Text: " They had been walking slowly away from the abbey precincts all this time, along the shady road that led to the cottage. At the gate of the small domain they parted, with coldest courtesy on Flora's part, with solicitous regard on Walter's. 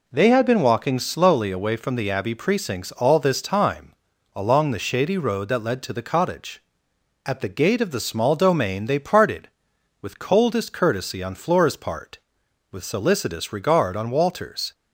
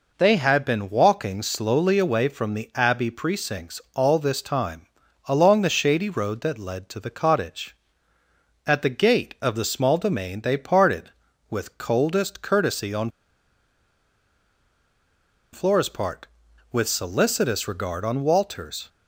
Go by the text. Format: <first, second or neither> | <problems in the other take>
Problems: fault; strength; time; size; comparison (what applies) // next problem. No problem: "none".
first | pauses between "on" and "Flora's"; strong; at 13.1 s; 2.4 s long